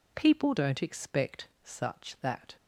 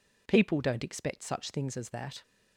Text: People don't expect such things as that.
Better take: second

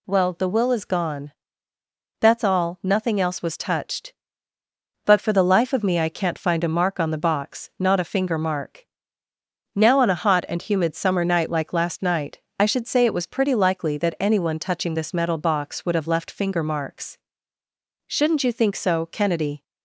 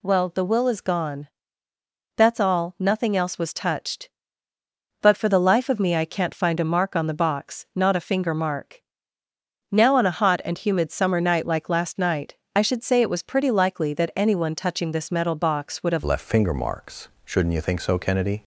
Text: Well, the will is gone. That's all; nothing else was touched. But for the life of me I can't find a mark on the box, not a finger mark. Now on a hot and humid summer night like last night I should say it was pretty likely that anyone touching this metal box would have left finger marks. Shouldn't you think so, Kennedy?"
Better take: first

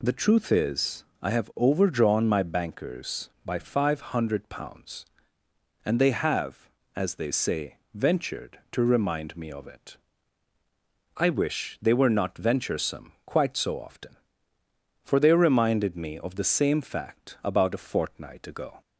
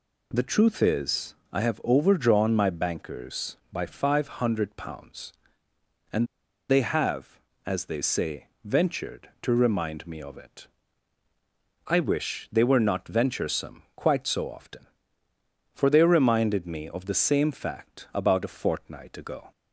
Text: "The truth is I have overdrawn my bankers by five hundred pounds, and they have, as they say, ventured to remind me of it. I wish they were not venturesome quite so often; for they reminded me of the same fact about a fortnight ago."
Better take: first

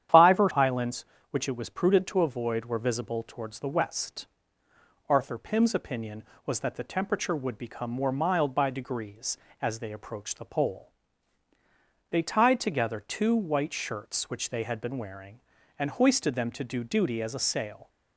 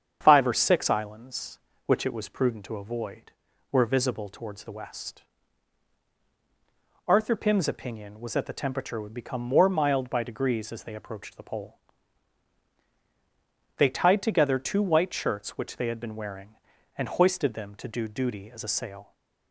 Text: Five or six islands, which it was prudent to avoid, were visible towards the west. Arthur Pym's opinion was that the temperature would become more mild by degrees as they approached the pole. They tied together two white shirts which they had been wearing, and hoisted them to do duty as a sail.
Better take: second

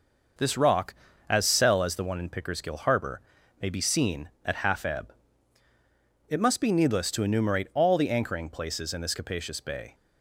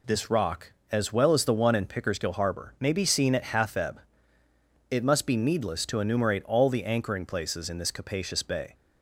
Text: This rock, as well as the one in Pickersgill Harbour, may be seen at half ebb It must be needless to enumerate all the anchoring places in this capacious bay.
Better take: second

